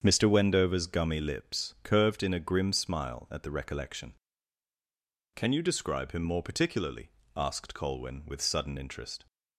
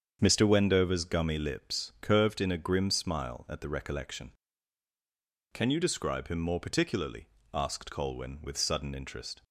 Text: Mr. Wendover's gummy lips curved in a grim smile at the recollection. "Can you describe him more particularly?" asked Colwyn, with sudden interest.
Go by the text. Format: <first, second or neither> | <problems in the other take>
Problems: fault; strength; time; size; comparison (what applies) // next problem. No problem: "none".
neither | starts louder than the rest; strong; the same in both